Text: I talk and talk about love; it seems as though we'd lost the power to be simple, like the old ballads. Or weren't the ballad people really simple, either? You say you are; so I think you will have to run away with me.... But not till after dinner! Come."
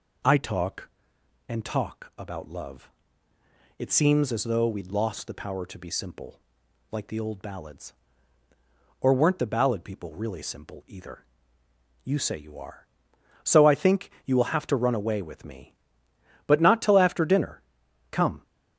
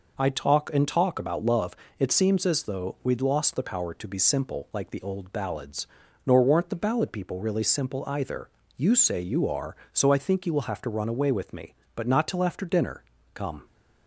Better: first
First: none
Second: says "Nor" for "Or"; at 6.2 s

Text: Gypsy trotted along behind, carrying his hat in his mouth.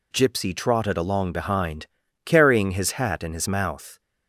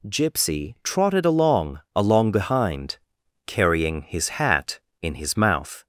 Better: first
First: none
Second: says "along" twice; at 1.9 s

